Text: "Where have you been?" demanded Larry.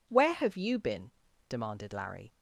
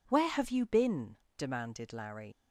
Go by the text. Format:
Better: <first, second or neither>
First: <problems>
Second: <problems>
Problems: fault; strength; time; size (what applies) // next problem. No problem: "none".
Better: first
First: none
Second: leaves "Larry" unfinished; at 2.3 s; 75 ms